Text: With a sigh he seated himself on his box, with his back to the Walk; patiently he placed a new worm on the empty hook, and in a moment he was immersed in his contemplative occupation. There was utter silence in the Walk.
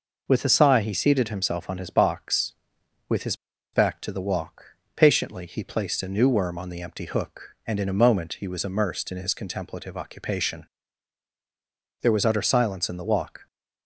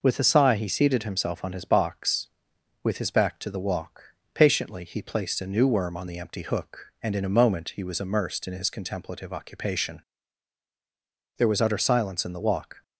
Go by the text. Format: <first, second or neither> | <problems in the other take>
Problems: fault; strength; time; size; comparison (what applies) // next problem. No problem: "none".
second | pauses between "his" and "back"; at 3.3 s; 0.39 s long